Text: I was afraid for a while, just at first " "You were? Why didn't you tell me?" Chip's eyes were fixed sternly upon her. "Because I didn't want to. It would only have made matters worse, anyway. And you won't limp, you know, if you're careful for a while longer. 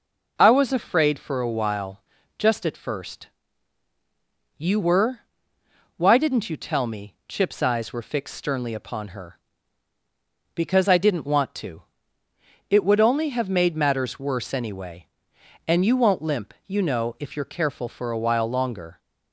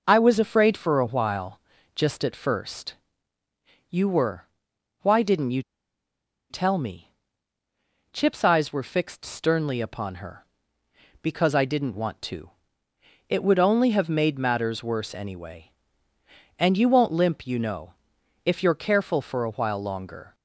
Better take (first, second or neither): first